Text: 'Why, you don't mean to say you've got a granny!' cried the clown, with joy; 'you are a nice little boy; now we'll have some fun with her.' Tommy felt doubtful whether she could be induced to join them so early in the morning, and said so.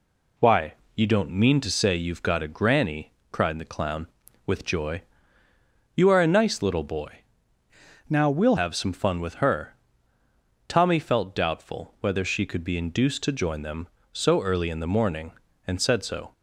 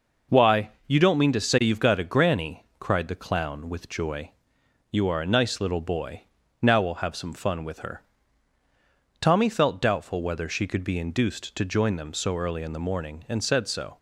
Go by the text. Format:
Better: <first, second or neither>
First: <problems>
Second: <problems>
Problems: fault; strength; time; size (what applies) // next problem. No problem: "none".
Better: second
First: changes voice from "now" to "we'll"; from 8.0 to 8.5 s; 0.5 s long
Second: none